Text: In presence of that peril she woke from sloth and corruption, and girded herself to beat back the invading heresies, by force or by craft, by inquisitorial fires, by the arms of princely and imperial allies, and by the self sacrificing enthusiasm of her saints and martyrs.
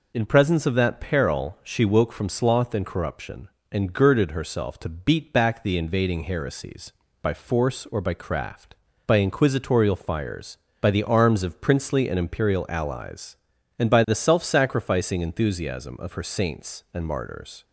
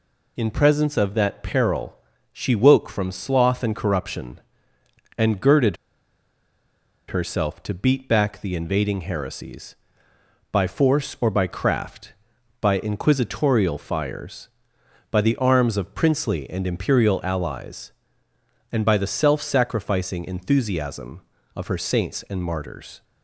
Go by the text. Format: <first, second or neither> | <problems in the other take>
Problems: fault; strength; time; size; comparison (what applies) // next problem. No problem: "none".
first | pauses between "peril" and "she"; slight; at 1.9 s; 0.34 s long // pauses between "girded" and "herself"; strong; at 5.7 s; 1.3 s long